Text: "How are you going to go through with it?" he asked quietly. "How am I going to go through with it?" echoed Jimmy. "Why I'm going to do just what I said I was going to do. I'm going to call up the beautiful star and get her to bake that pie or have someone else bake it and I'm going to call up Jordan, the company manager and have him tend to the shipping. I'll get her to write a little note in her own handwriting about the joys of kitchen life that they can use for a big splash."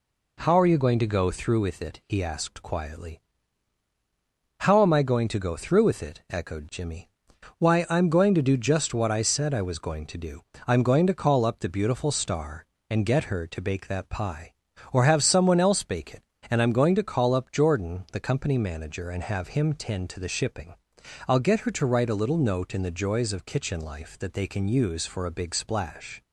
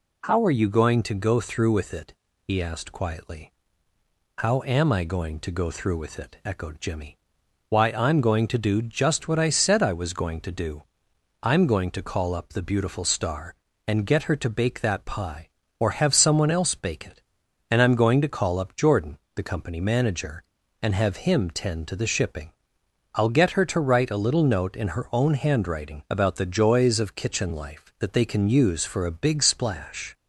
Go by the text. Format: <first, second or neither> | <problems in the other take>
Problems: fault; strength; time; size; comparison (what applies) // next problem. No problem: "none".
second | skips "her own handwriting about"; at 22.8 s